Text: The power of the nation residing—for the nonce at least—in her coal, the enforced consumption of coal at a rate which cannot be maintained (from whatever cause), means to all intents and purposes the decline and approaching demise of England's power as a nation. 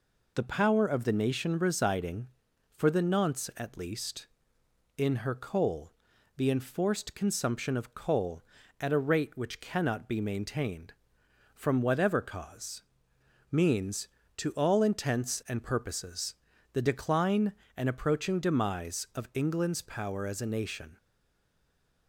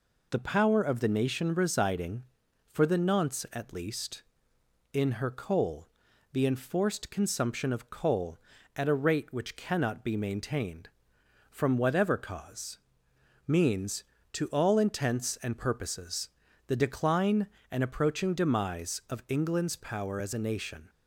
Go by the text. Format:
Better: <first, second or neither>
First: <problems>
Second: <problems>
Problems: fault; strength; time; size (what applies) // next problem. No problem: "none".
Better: second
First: pauses between "purposes" and "the"; at 16.3 s; 0.38 s long // stays silent after the last word; from 20.9 s on; 1.1 s long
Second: pauses between "purposes" and "the"; at 16.2 s; 0.38 s long